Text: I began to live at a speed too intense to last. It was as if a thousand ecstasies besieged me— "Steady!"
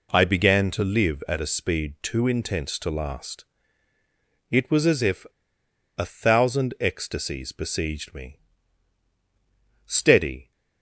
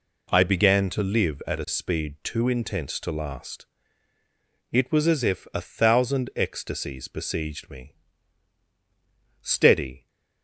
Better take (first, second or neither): second